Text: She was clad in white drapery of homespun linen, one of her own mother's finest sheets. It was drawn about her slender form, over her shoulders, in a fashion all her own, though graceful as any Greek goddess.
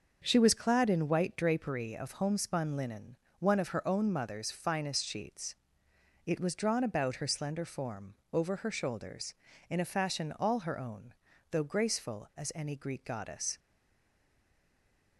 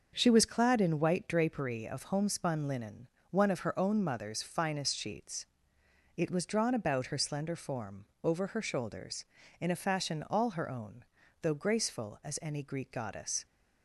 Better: second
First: starts louder than the rest; until 1.2 s; 6.5 dB // stays silent after the last word; noticeable; from 13.5 s on; 1.6 s long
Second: starts louder than the rest; until 1.1 s; 6.5 dB

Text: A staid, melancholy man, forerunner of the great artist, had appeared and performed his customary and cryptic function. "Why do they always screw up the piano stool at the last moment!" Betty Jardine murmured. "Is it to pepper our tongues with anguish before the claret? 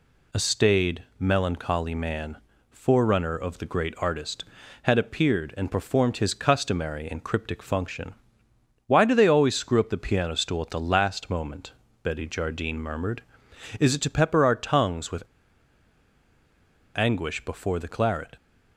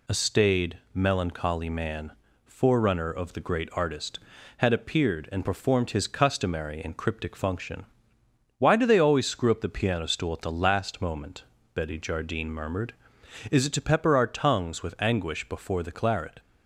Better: second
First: pauses between "with" and "anguish"; strong; at 15.2 s; 1.7 s long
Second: none

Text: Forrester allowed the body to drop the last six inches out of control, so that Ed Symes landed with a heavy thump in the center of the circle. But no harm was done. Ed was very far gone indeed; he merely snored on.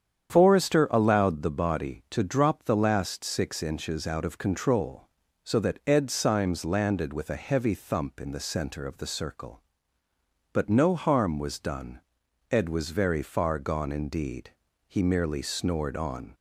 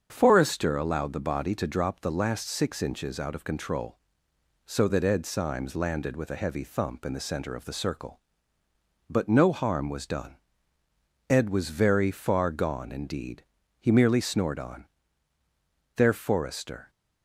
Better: first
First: starts louder than the rest; strong; until 1.3 s; 8.5 dB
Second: starts louder than the rest; strong; until 1.1 s; 7 dB // goes on to say "There Forrester"; noticeable; from 15.9 s on; 0.96 s long

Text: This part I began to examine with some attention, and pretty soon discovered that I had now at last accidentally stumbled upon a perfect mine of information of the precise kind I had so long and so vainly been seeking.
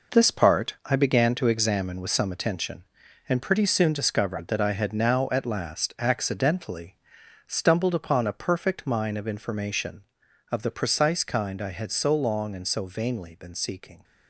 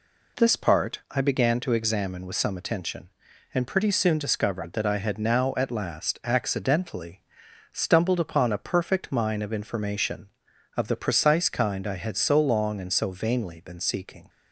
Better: second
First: gets quieter; strong; throughout; 8.5 dB // pauses between "accidentally" and "stumbled"; noticeable; at 6.9 s; 0.50 s long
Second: pauses between "accidentally" and "stumbled"; noticeable; at 7.2 s; 0.50 s long

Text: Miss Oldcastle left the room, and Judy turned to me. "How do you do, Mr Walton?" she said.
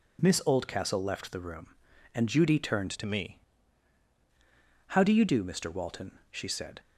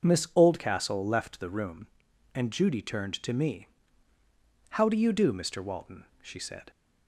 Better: second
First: changes voice from "to" to "me"; from 2.9 to 3.3 s; 0.4 s long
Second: none

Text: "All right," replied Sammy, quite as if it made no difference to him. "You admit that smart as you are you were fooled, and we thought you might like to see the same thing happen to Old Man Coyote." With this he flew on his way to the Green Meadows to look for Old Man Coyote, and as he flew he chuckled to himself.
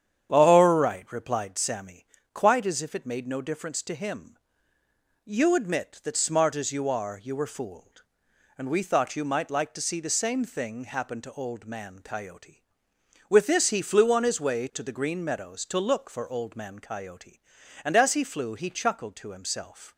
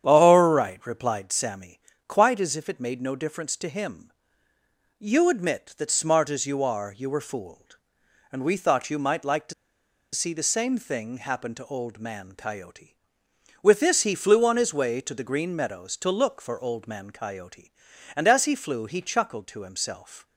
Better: first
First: starts louder than the rest; strong; until 1.3 s; 9 dB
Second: starts louder than the rest; strong; until 1.1 s; 9 dB // pauses between "to" and "see"; noticeable; at 9.5 s; 0.60 s long

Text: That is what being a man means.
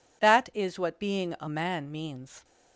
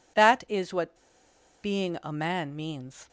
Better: first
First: none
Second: pauses between "what" and "being"; noticeable; at 0.9 s; 0.68 s long

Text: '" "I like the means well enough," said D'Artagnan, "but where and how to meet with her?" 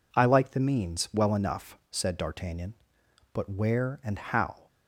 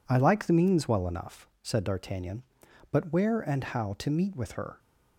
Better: second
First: stops before "to meet with her"; at 4.6 s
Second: none

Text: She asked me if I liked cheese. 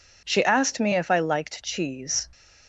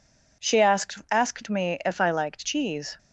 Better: first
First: none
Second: says "asked" twice; at 1.1 s

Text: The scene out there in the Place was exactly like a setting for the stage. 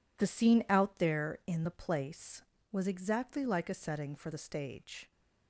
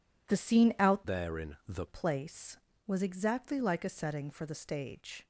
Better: first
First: none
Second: changes voice from "there" to "the"; from 1.0 to 1.8 s; 0.8 s long

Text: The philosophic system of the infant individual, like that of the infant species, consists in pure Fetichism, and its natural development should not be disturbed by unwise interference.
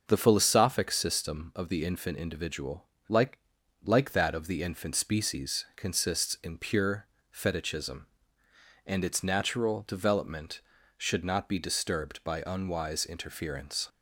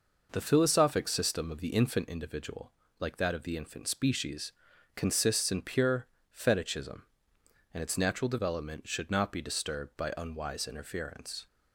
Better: second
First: starts louder than the rest; noticeable; until 1.0 s; 6 dB // says "like" twice; at 3.8 s // pauses between "pure" and "Fetichism"; slight; at 7.0 s; 0.26 s long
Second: pauses between "pure" and "Fetichism"; slight; at 6.0 s; 0.26 s long

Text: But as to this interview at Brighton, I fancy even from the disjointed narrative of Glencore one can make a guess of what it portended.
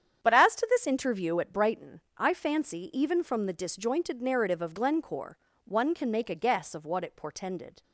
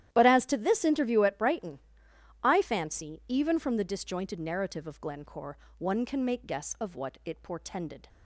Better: first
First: starts louder than the rest; strong; until 1.2 s; 8.5 dB // pauses between "Glencore" and "one"; slight; at 5.3 s; 0.28 s long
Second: starts louder than the rest; strong; until 1.1 s; 12 dB // pauses between "Glencore" and "one"; slight; at 5.5 s; 0.22 s long // skips "a"; at 6.4 s

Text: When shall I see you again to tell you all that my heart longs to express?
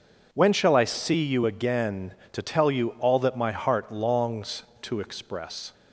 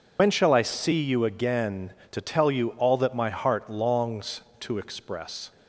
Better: first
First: none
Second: loses the start of "When"; at 0.1 s; 90 ms

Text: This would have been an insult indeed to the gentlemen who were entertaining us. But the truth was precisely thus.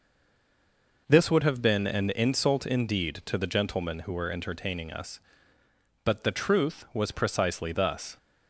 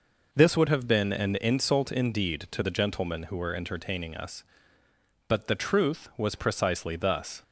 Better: second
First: stays silent before the first word; until 1.0 s; 1.0 s long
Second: none

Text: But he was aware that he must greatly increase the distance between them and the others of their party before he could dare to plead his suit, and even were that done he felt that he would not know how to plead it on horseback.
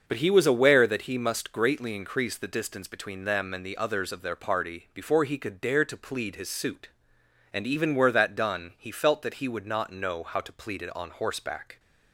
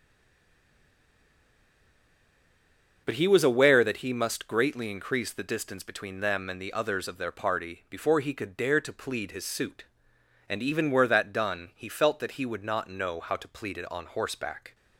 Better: first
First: starts louder than the rest; until 1.0 s; 6.5 dB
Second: stays silent before the first word; strong; until 3.0 s; 3.0 s long // starts louder than the rest; until 4.0 s; 6.5 dB

